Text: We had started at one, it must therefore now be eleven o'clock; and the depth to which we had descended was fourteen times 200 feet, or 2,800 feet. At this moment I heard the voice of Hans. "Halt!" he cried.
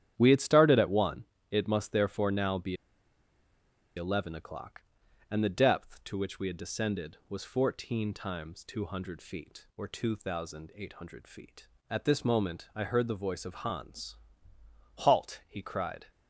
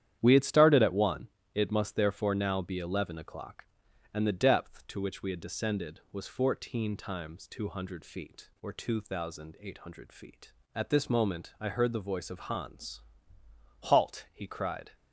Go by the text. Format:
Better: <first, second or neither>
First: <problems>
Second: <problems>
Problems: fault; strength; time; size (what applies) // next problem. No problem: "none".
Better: second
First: starts louder than the rest; strong; until 1.1 s; 10.5 dB // pauses between "be" and "eleven"; at 2.7 s; 1.2 s long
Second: starts louder than the rest; strong; until 1.2 s; 10.5 dB